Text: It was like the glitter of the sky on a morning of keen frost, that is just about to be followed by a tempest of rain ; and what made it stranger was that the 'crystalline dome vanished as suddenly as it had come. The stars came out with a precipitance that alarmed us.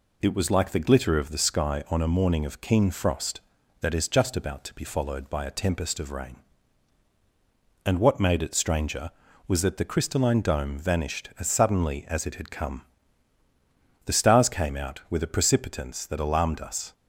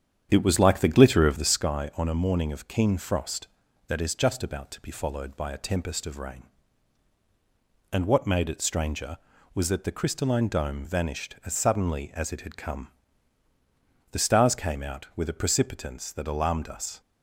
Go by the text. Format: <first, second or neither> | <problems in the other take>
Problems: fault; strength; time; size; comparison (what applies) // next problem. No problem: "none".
first | starts louder than the rest; strong; until 1.7 s; 8.5 dB